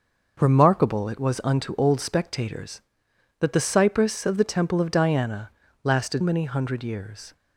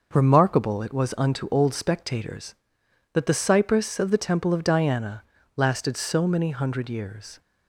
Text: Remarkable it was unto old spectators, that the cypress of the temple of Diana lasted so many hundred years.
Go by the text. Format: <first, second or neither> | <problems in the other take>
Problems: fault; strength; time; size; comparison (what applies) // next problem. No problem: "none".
second | starts louder than the rest; noticeable; until 1.4 s; 6 dB // pauses between "Diana" and "lasted"; slight; at 5.5 s; 0.32 s long; slight in the second // skips "so"; at 6.2 s